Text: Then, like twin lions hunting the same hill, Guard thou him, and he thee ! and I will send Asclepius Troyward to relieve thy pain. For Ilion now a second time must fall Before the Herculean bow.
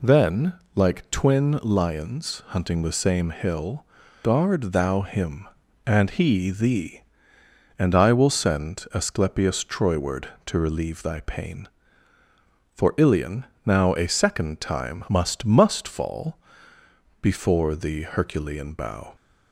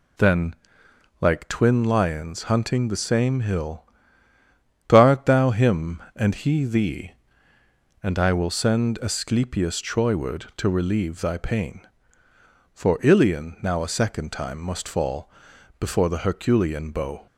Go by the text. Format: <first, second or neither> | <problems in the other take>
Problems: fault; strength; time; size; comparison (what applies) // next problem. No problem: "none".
second | pauses between "Ilion" and "now"; slight; at 13.4 s; 0.20 s long // says "must" twice; at 15.4 s // pauses between "fall" and "Before"; noticeable; at 16.3 s; 0.82 s long; noticeable in the second